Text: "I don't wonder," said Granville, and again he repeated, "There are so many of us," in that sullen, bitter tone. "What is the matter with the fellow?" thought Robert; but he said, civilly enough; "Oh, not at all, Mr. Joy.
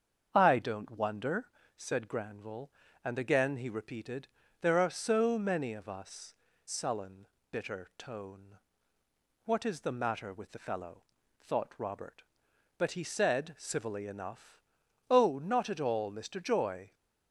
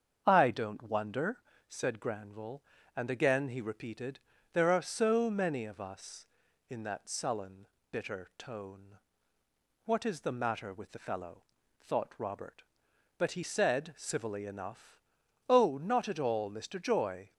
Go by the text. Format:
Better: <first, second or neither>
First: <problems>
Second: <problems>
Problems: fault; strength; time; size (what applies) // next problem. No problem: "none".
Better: second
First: starts louder than the rest; strong; until 1.3 s; 7 dB // skips "in that"; at 6.5 s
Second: starts louder than the rest; strong; until 1.2 s; 7 dB